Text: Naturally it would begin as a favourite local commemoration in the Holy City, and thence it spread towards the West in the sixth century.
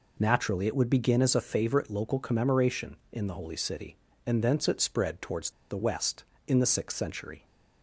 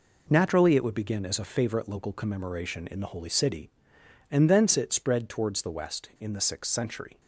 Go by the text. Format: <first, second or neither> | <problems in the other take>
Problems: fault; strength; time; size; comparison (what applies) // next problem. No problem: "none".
second | pauses between "towards" and "the"; slight; at 5.5 s; 0.19 s long